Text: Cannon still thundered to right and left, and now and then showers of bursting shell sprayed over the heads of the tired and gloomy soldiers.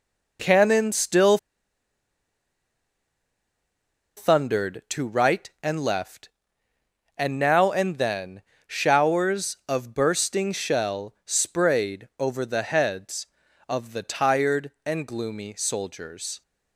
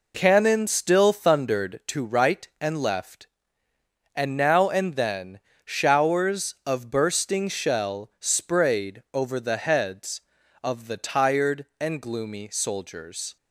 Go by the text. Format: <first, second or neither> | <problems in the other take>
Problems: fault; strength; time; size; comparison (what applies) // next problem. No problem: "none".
second | pauses between "still" and "thundered"; strong; at 1.3 s; 2.8 s long // pauses between "then" and "showers"; slight; at 8.4 s; 0.26 s long; slight in the second